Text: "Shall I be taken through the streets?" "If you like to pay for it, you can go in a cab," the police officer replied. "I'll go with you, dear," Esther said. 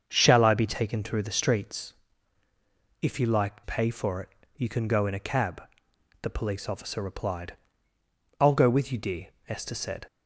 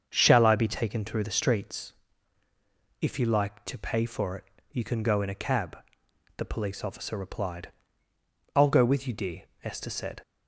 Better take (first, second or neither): second